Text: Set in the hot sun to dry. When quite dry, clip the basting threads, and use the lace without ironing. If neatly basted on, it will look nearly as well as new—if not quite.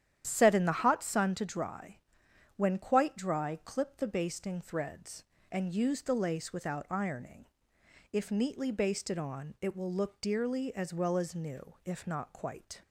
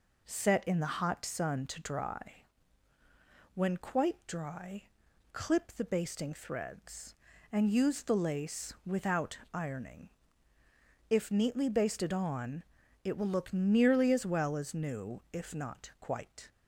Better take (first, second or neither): second